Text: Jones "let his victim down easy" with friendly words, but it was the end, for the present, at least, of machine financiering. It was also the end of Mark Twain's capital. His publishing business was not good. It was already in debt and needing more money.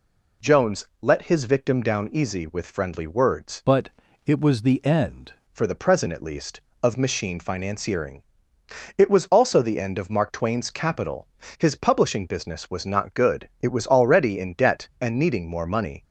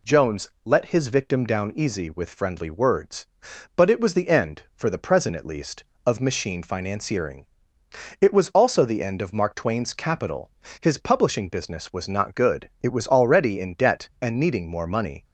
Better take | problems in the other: second | pauses between "Jones" and "let"; slight; at 0.8 s; 0.16 s long; slight in the second // changes voice from "but" to "end"; from 3.6 to 5.3 s; 1.7 s long // pauses between "but" and "it"; at 3.8 s; 0.38 s long

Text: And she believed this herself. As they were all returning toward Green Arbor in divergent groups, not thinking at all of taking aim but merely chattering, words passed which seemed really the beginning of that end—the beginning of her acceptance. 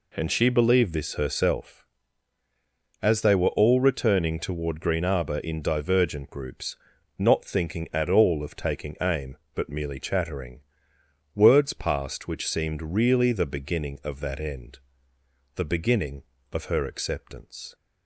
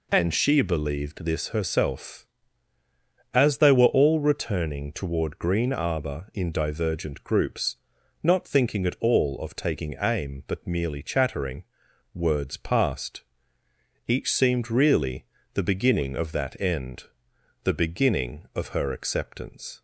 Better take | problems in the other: first | says "each" for "which"; at 14.1 s // pauses between "really" and "the"; slight; at 15.2 s; 0.26 s long

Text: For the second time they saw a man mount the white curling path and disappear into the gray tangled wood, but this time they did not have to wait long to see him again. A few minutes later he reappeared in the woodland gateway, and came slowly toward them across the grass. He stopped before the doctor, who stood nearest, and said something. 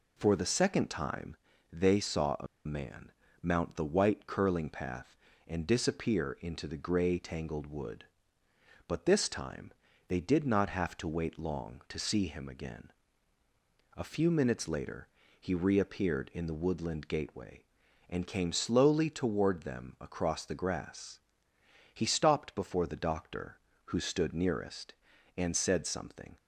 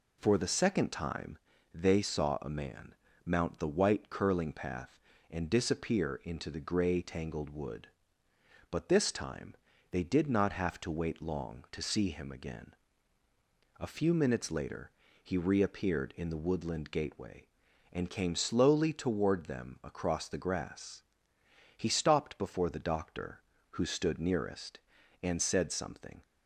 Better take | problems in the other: second | pauses between "time" and "they"; slight; at 1.3 s; 0.36 s long; slight in the second // pauses between "a" and "man"; slight; at 2.4 s; 0.19 s long // pauses between "man" and "mount"; slight; at 3.1 s; 0.30 s long; slight in the second // pauses between "time" and "they"; slight; at 9.7 s; 0.36 s long; slight in the second // pauses between "later" and "he"; slight; at 15.0 s; 0.32 s long; slight in the second

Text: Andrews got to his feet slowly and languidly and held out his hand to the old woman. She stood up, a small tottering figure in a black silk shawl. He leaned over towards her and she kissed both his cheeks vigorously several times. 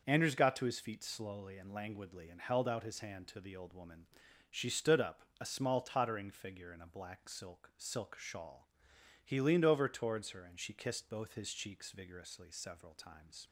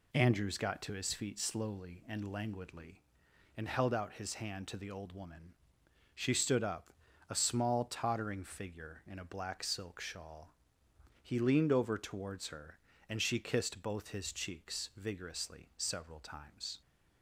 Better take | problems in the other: second | starts louder than the rest; until 1.0 s; 6 dB // says "silk" twice; at 7.7 s

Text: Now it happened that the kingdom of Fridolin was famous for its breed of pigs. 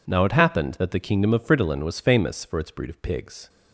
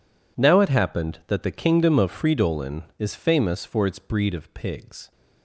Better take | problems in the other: first | says "is" for "was"; at 2.9 s

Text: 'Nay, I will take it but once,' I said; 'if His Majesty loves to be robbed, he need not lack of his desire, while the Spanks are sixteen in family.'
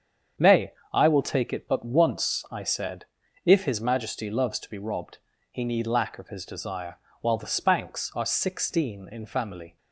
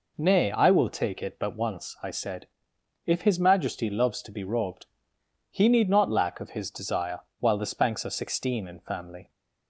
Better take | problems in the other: second | starts louder than the rest; strong; until 1.5 s; 7.5 dB // skips "not"; at 5.8 s

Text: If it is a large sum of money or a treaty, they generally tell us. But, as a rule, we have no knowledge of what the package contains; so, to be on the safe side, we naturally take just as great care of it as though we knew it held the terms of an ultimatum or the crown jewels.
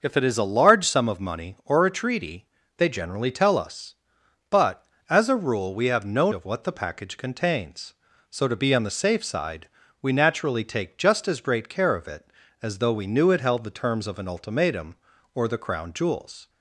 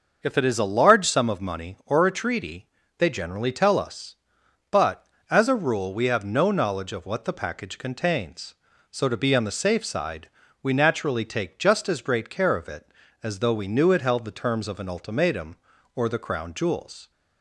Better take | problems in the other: second | skips "knowledge"; at 6.3 s

